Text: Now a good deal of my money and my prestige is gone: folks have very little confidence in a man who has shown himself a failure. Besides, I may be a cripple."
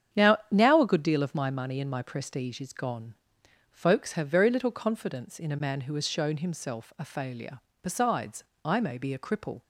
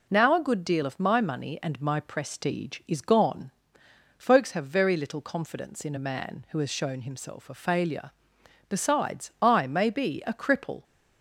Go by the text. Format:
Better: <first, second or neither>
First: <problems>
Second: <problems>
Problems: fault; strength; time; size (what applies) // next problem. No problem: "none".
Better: second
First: starts louder than the rest; strong; until 1.2 s; 8.5 dB // says "Now" twice; at 0.4 s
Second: none